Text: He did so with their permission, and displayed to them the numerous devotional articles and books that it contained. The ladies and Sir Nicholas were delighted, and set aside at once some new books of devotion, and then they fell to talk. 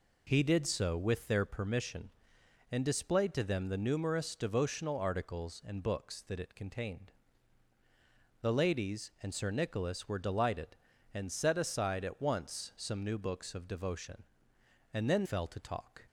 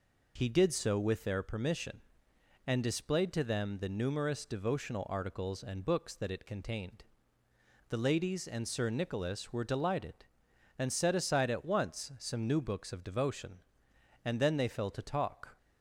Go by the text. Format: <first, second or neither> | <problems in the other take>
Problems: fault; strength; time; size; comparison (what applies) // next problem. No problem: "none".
second | skips "they"; at 15.2 s